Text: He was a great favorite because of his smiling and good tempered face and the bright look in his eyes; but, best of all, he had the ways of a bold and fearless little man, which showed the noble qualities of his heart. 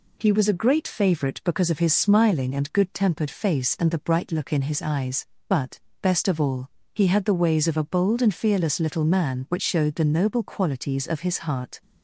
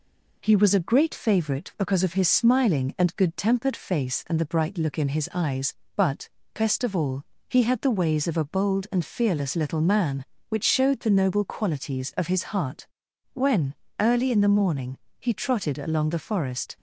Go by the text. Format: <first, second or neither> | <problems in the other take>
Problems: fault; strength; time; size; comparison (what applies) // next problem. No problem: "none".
first | goes on to say "When early in the morning he trotted along the forest"; strong; from 13.3 s on; 3.4 s long